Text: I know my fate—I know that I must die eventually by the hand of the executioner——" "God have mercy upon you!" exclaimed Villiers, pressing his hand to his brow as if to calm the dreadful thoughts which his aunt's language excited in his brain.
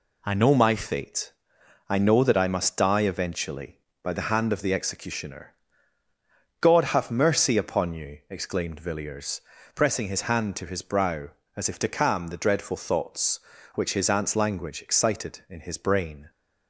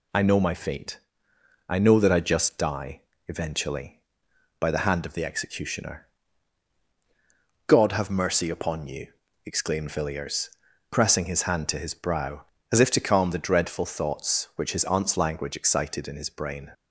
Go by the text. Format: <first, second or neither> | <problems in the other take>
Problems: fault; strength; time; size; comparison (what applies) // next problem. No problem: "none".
first | says "just" for "must"; at 2.1 s // pauses between "die" and "eventually"; slight; at 3.0 s; 0.26 s long